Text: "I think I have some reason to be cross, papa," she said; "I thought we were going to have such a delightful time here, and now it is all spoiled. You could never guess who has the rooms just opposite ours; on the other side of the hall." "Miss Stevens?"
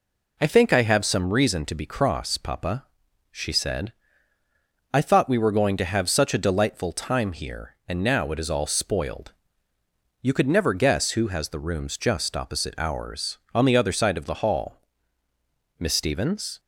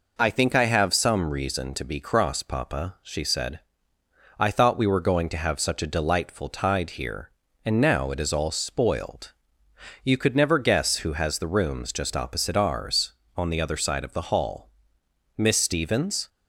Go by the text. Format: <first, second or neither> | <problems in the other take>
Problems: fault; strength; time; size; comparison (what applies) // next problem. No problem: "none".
first | says "tide" for "time"; at 6.4 s